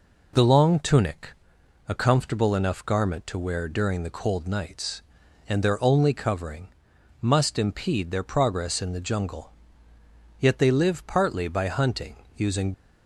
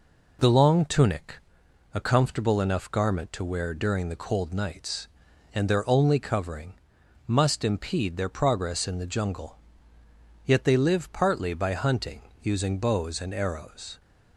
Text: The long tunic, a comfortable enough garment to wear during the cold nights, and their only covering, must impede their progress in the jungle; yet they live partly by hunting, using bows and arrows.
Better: second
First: stops before "bows and arrows"; at 12.7 s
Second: none

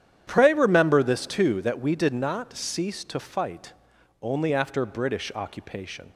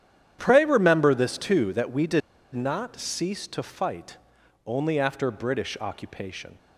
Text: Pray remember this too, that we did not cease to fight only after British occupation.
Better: first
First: starts louder than the rest; strong; until 1.2 s; 10 dB // pauses between "fight" and "only"; noticeable; at 3.7 s; 0.50 s long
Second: starts louder than the rest; strong; until 1.4 s; 9.5 dB // pauses between "did" and "not"; slight; at 2.2 s; 0.34 s long // pauses between "fight" and "only"; noticeable; at 4.1 s; 0.50 s long

